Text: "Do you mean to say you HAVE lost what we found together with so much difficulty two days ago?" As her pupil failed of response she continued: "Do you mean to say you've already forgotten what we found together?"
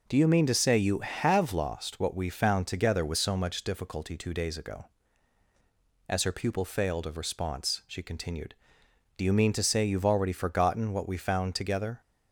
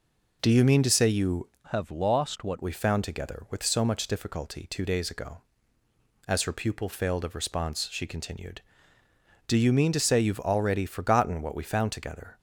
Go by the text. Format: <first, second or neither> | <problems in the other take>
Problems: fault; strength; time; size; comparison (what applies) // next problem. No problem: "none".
first | changes voice from "HAVE" to "what"; from 1.6 to 2.5 s; 0.9 s long